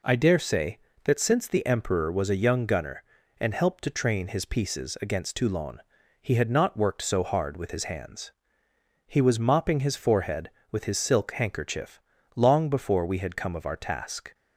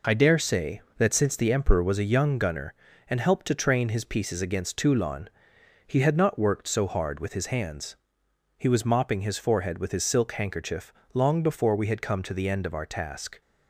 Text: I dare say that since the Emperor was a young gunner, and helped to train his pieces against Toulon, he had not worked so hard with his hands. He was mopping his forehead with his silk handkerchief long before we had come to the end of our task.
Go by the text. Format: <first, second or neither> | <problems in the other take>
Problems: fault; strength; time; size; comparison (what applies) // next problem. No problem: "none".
second | pauses between "handkerchief" and "long"; slight; at 11.9 s; 0.36 s long; slight in the second // skips "to the end"; at 13.5 s